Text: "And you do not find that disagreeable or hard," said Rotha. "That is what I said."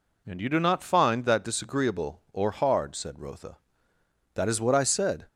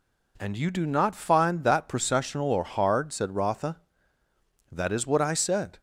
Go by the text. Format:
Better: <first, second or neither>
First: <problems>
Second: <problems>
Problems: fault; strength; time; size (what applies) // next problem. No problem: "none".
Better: first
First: none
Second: says "processional" for "disagreeable"; at 1.8 s